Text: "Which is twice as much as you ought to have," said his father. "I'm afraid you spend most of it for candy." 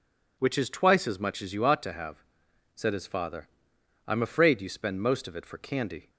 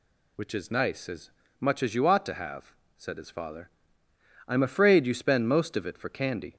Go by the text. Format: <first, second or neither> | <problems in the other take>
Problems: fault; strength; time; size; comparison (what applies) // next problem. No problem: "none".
first | says "nice" for "twice"; at 0.7 s // pauses between "as" and "much"; slight; at 1.2 s; 0.30 s long